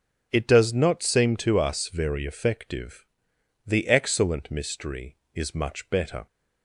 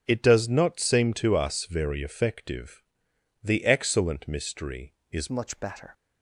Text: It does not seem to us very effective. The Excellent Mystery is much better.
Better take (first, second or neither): first